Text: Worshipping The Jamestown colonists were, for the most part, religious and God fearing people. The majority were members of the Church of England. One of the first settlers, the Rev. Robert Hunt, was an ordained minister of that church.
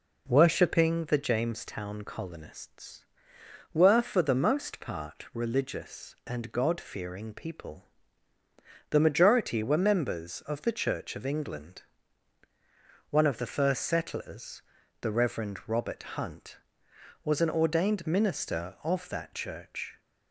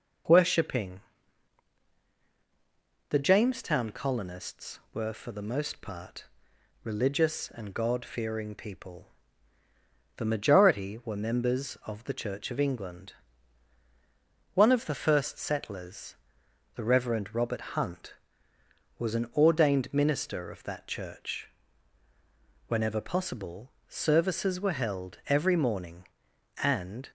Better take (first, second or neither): first